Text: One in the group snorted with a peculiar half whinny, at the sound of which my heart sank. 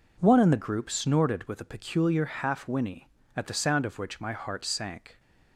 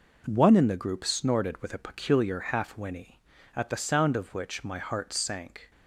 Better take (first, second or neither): neither